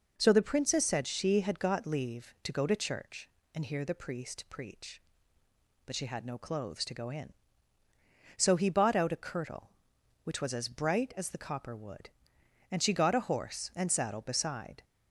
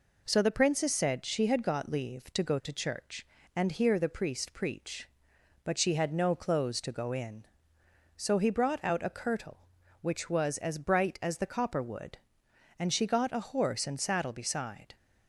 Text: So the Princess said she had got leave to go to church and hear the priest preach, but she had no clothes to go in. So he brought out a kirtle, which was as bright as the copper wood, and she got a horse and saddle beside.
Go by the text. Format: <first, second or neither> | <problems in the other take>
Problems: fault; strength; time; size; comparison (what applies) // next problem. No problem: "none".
second | says "bought" for "brought"; at 8.6 s